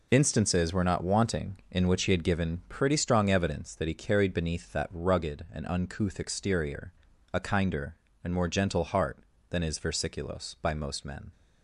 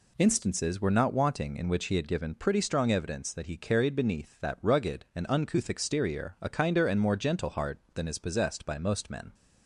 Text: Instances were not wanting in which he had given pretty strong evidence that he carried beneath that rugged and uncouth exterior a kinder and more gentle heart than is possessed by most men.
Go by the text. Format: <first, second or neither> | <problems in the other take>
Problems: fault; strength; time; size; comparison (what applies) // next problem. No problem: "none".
second | pauses between "exterior" and "a"; at 6.9 s; 0.42 s long // says "versiculos" for "possessed"; at 9.7 s